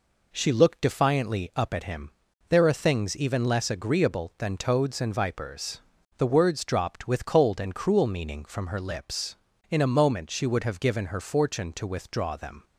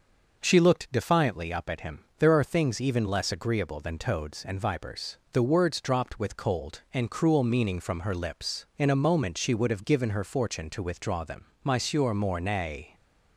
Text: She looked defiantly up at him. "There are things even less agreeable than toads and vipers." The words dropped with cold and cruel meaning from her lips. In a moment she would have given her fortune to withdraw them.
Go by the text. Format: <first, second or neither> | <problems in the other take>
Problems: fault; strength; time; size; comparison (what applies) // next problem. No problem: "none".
first | starts louder than the rest; noticeable; until 1.4 s; 6 dB // goes on to say "Monsieur Mornay"; noticeable; from 11.6 s on; 1.3 s long